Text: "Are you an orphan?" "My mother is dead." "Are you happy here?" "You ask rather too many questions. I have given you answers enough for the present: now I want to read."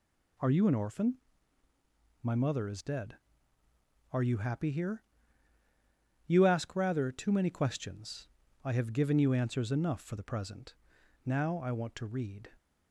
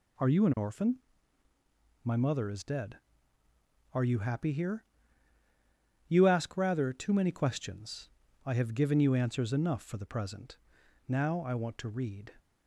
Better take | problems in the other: neither | none

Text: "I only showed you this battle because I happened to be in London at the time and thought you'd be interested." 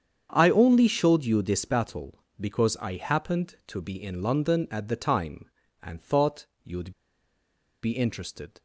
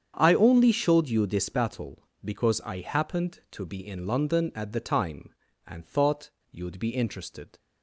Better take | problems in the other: second | starts louder than the rest; strong; until 1.3 s; 8 dB; strong in the second // pauses between "thought" and "you'd"; slight; at 6.4 s; 0.16 s long; slight in the second // pauses between "you'd" and "be"; noticeable; at 6.9 s; 0.90 s long

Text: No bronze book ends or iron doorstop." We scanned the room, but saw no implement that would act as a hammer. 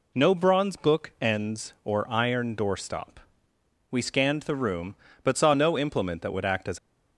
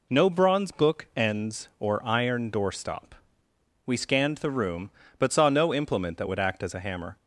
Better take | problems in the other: second | stops before "a hammer"; at 6.7 s

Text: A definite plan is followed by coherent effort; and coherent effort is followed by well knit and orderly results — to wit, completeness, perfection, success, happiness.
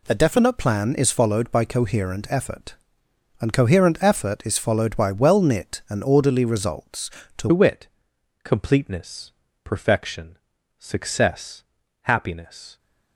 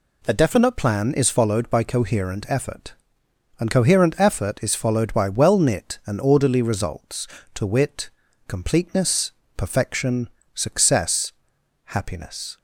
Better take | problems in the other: second | changes voice at "wit"; from 7.5 s on; 5.2 s long

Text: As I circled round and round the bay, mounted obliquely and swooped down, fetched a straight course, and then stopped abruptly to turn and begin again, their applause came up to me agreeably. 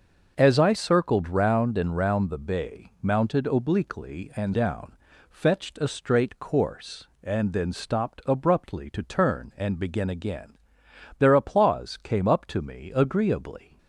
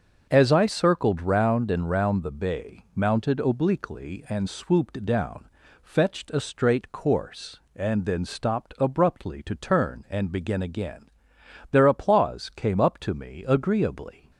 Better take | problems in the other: second | starts louder than the rest; until 1.3 s; 6.5 dB; also in the second // skips "swooped"; at 4.5 s

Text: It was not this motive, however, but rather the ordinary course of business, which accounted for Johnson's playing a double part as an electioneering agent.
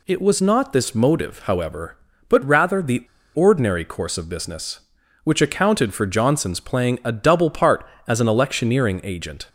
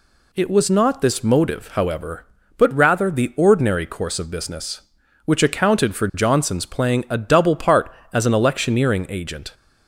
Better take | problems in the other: second | pauses between "the" and "ordinary"; slight; at 3.0 s; 0.29 s long

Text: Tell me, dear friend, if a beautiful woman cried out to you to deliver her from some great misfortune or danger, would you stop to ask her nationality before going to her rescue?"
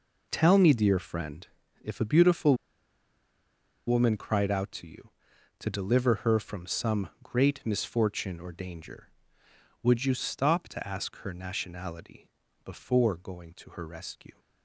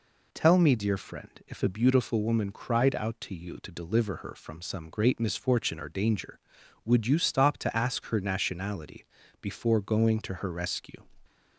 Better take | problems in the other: second | pauses between "beautiful" and "woman"; strong; at 2.5 s; 1.3 s long // pauses between "nationality" and "before"; slight; at 12.2 s; 0.34 s long; slight in the second

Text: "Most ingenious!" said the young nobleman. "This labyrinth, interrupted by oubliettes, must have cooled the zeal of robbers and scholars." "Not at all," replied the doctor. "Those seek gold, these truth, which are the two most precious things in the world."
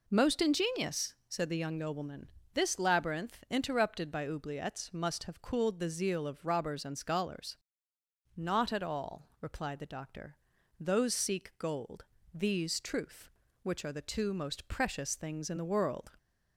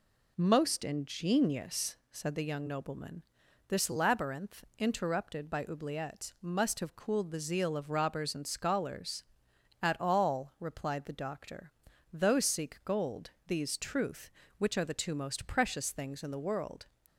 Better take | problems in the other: first | skips "Not"; at 9.5 s

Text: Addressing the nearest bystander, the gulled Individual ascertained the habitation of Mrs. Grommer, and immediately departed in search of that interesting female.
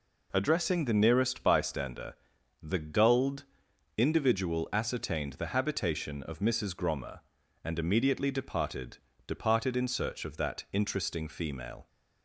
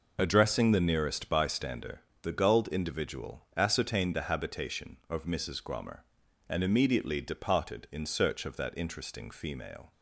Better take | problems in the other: second | pauses between "gulled" and "Individual"; noticeable; at 3.4 s; 0.54 s long // says "departed" twice; at 9.2 s

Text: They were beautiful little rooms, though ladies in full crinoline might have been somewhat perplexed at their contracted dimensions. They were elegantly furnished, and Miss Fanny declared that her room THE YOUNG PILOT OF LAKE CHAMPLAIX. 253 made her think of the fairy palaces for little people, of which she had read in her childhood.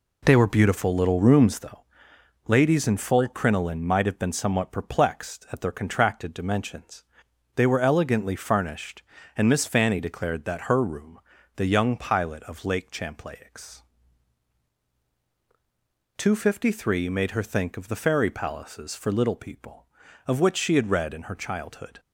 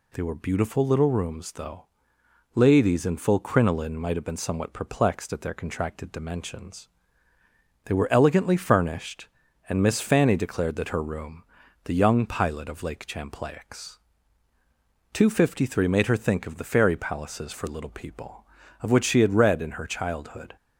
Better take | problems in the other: second | starts louder than the rest; slight; until 1.9 s; 3 dB // pauses between "though" and "ladies"; noticeable; at 1.7 s; 0.66 s long; noticeable in the second // pauses between "room" and "THE"; slight; at 11.1 s; 0.36 s long; also in the second

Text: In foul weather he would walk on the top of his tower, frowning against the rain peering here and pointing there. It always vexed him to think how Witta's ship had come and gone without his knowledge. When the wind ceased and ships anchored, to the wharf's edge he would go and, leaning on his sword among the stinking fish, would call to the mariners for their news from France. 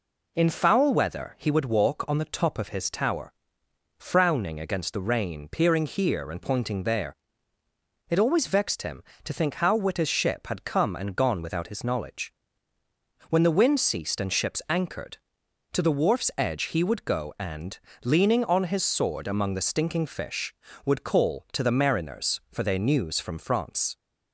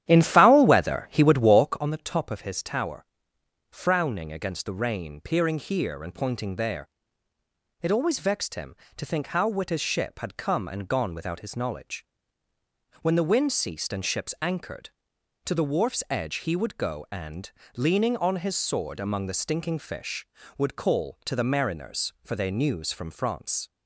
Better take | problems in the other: first | starts louder than the rest; strong; until 1.8 s; 11 dB

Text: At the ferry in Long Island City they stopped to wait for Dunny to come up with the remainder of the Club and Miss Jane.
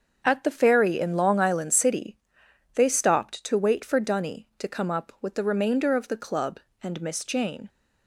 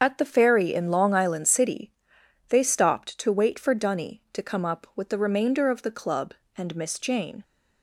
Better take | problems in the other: first | loses the start of "At"; at 0.0 s; 25 ms // starts louder than the rest; until 1.0 s; 6.5 dB; also in the first // pauses between "City" and "they"; noticeable; at 1.9 s; 0.58 s long; noticeable in the first

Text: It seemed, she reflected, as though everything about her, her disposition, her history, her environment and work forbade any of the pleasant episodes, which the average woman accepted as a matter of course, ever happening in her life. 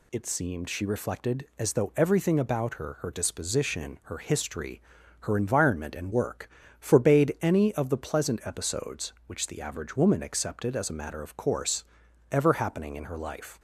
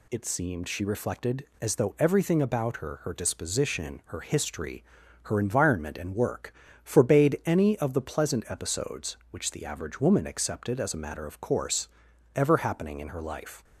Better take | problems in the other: neither | pauses between "work" and "forbade"; slight; the same in both

